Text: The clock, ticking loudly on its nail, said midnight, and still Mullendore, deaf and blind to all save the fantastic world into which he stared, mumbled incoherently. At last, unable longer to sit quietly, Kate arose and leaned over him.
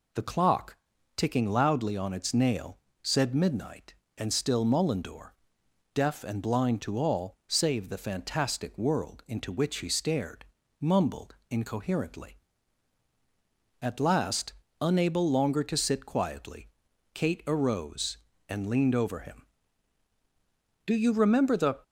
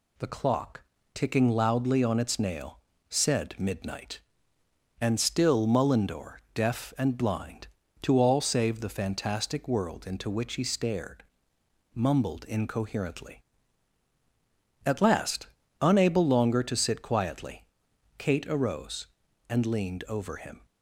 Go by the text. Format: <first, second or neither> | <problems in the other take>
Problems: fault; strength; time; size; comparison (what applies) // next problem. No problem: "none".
second | goes on to say "Do you remember the"; noticeable; from 20.8 s on; 0.94 s long